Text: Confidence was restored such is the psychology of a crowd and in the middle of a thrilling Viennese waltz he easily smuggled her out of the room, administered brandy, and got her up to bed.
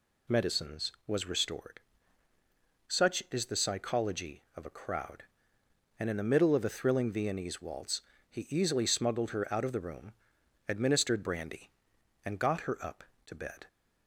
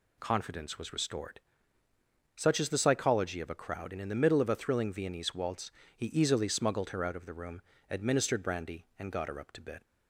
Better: second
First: says "Medicines" for "Confidence"; at 0.2 s // pauses between "restored" and "such"; at 1.7 s; 1.1 s long // pauses between "waltz" and "he"; slight; at 8.0 s; 0.28 s long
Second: pauses between "restored" and "such"; noticeable; at 1.3 s; 0.96 s long // pauses between "waltz" and "he"; slight; at 5.7 s; 0.24 s long

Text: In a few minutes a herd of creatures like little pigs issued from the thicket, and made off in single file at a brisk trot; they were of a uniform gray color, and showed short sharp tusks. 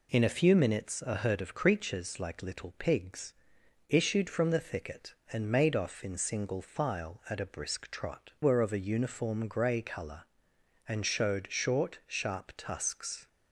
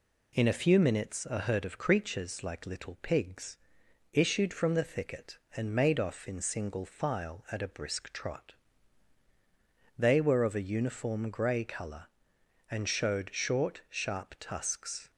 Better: second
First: pauses between "pigs" and "issued"; noticeable; at 3.3 s; 0.56 s long // skips "they"; at 8.3 s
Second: pauses between "pigs" and "issued"; noticeable; at 3.5 s; 0.56 s long

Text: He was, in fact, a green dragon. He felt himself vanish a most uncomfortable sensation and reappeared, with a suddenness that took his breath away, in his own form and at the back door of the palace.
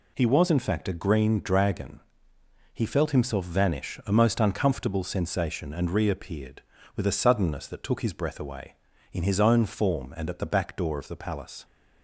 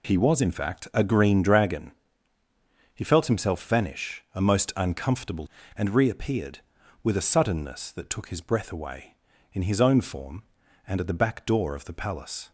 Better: first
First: none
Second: skips "sensation"; at 5.6 s

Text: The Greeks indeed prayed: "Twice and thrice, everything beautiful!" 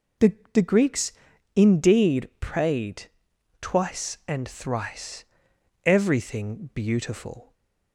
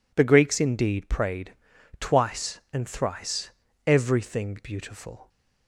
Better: second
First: says "The" twice; at 0.5 s // pauses between "Greeks" and "indeed"; at 1.1 s; 0.42 s long // stays silent after the last word; slight; from 7.4 s on; 0.5 s long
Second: none

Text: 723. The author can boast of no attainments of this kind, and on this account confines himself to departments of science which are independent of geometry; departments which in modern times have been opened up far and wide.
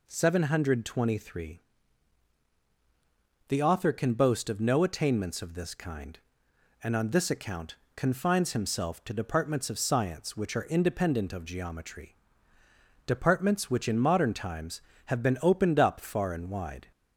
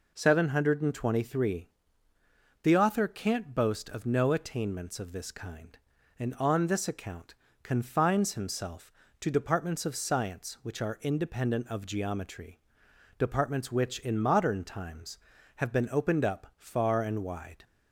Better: first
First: pauses between "account" and "confines"; slight; at 7.7 s; 0.22 s long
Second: says "can't" for "can"; at 3.0 s // pauses between "account" and "confines"; slight; at 7.3 s; 0.30 s long

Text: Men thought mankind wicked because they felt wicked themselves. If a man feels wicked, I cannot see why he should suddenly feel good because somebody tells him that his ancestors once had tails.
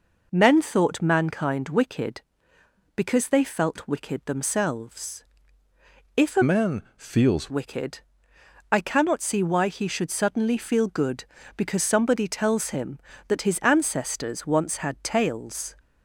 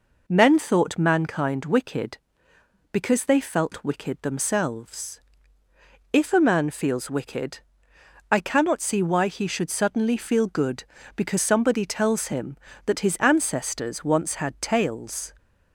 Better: second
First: changes voice from "man" to "feels"; from 6.4 to 7.4 s; 1.0 s long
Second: none

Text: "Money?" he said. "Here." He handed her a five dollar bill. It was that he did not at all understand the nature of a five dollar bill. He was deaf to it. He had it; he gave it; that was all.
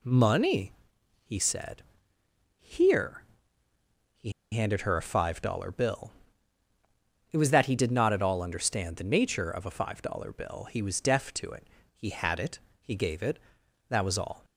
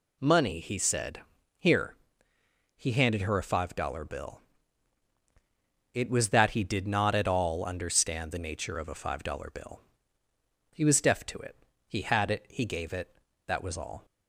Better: second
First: pauses between "He" and "handed"; slight; at 4.2 s; 0.22 s long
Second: none

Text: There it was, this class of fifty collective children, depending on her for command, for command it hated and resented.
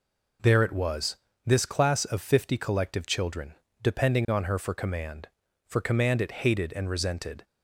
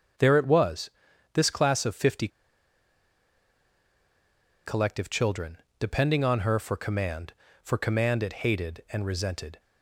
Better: first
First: none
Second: starts louder than the rest; until 1.5 s; 6.5 dB // pauses between "fifty" and "collective"; strong; at 2.2 s; 2.3 s long

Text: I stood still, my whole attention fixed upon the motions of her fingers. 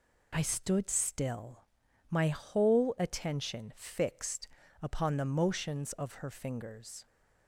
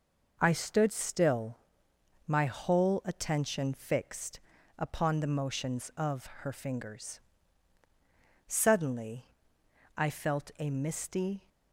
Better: first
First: pauses between "fixed" and "upon"; slight; at 4.4 s; 0.34 s long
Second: pauses between "fixed" and "upon"; at 4.3 s; 0.40 s long // pauses between "of" and "her"; slight; at 6.2 s; 0.16 s long // goes on to say "Suddenly I felt a misty"; strong; from 8.4 s on; 3.0 s long

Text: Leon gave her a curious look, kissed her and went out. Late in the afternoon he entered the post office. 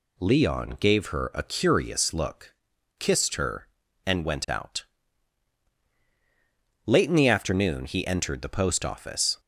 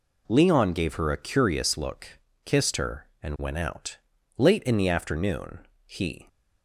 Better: first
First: none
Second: pauses between "afternoon" and "he"; slight; at 5.5 s; 0.26 s long // stops before "entered the post office"; at 6.2 s

